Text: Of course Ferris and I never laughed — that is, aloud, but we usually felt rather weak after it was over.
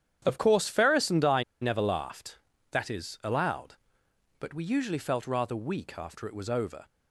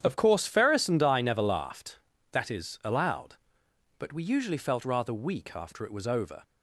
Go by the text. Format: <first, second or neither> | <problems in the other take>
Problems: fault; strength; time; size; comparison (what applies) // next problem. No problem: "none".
second | starts louder than the rest; strong; until 1.2 s; 9.5 dB; strong in the second // pauses between "I" and "never"; slight; at 1.4 s; 0.18 s long